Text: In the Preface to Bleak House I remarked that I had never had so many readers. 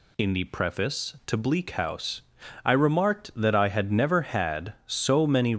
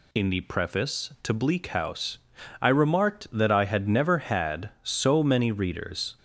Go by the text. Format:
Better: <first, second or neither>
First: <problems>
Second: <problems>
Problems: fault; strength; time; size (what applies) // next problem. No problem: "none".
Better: second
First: pauses between "House" and "I"; at 2.2 s; 0.44 s long // stops before "readers"; at 5.5 s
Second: pauses between "House" and "I"; at 2.1 s; 0.44 s long